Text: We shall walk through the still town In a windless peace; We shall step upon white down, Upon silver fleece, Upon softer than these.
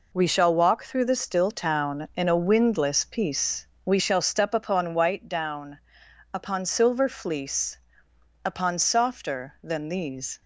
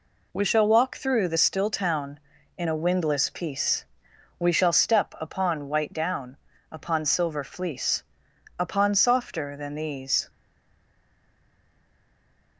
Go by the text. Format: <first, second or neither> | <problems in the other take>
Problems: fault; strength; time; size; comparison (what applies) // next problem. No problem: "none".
first | stays silent after the last word; from 10.2 s on; 2.3 s long